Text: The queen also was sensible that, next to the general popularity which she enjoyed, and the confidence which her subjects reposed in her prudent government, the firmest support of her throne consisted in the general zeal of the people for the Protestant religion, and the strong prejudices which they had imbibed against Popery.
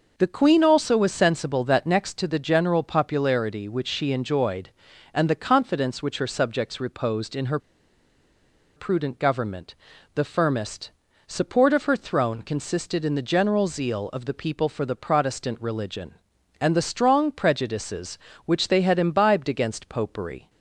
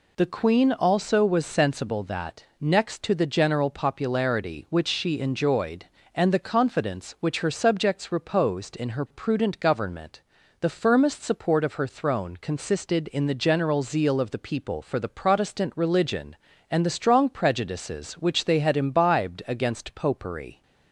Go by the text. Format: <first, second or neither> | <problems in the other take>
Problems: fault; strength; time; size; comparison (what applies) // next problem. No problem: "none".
second | pauses between "her" and "prudent"; at 7.5 s; 1.1 s long // pauses between "firmest" and "support"; at 10.8 s; 0.38 s long